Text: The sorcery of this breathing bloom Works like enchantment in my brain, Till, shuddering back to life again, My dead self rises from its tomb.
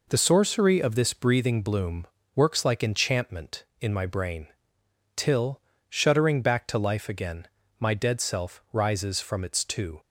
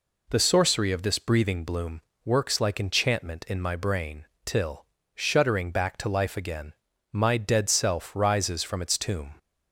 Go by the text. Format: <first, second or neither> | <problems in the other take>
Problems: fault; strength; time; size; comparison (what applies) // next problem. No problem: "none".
second | pauses between "bloom" and "Works"; slight; at 2.0 s; 0.28 s long; slight in the second // says "two" for "tomb"; at 9.6 s